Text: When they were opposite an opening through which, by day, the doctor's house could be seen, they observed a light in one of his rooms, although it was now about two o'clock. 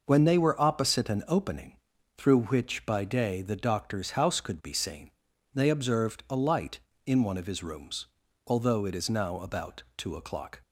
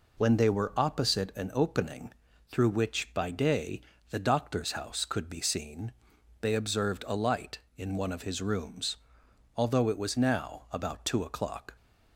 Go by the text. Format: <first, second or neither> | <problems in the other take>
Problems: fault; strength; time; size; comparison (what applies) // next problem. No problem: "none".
second | pauses between "opening" and "through"; at 1.7 s; 0.40 s long; also in the second // says "is" for "was"; at 8.9 s